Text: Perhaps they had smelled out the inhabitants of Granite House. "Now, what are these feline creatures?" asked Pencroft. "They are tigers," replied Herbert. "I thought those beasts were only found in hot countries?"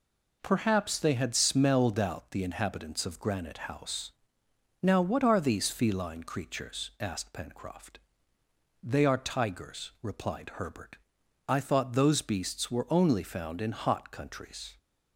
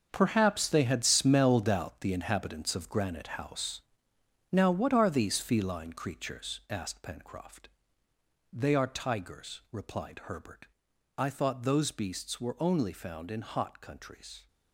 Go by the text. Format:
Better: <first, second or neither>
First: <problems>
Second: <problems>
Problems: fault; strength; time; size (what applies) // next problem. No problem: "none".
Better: first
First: none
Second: gets quieter; strong; throughout; 11.5 dB